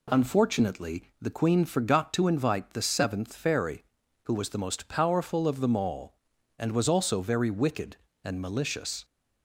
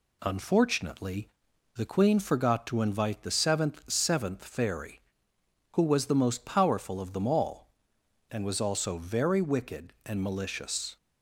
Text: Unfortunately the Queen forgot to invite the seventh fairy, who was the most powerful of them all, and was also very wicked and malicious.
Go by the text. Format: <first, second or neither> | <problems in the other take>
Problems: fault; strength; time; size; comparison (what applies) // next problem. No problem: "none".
first | pauses between "Unfortunately" and "the"; noticeable; at 1.2 s; 0.48 s long // says "seventh" twice; at 3.8 s